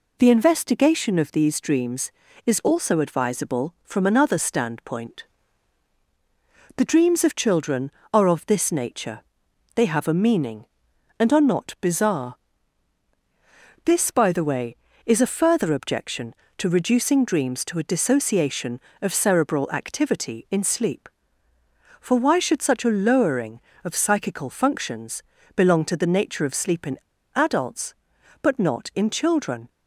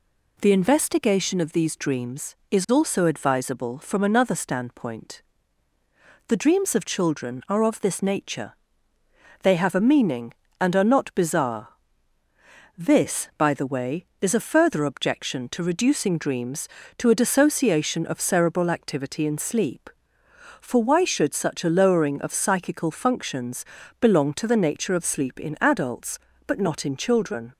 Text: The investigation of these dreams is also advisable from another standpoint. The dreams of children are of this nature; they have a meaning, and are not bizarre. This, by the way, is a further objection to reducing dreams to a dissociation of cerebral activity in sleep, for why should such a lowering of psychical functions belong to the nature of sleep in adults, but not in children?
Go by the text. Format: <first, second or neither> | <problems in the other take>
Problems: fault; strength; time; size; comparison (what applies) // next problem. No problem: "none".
second | pauses between "functions" and "belong"; slight; at 25.2 s; 0.34 s long; slight in the second // pauses between "in" and "adults"; at 26.9 s; 0.38 s long